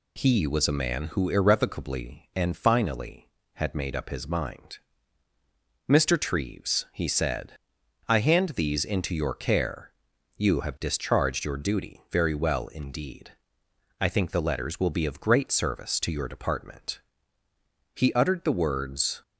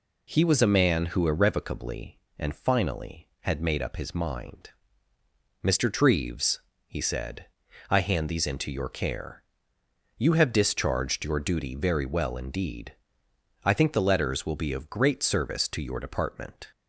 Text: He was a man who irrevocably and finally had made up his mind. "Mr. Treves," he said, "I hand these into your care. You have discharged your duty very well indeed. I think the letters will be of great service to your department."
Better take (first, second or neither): second